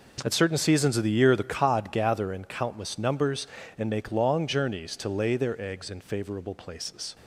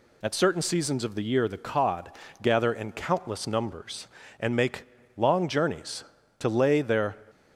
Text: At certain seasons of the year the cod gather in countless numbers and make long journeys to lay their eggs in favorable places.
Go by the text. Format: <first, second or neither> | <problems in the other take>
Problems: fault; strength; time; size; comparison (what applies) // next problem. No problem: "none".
first | pauses between "cod" and "gather"; slight; at 2.1 s; 0.32 s long // pauses between "make" and "long"; slight; at 4.8 s; 0.32 s long // stops before "eggs in favorable places"; at 7.2 s